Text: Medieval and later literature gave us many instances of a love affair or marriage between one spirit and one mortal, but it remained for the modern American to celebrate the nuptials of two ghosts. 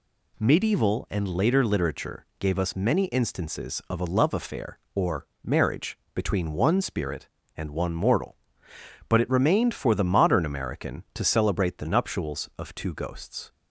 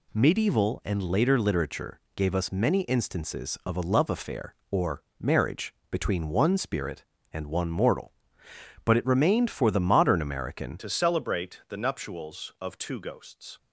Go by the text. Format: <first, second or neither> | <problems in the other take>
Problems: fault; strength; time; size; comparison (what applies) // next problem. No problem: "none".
first | pauses between "literature" and "gave"; slight; at 1.9 s; 0.16 s long // pauses between "or" and "marriage"; slight; at 5.0 s; 0.16 s long; slight in the first // pauses between "marriage" and "between"; slight; at 5.7 s; 0.20 s long; slight in the first // changes voice at "to"; from 10.7 s on; 2.8 s long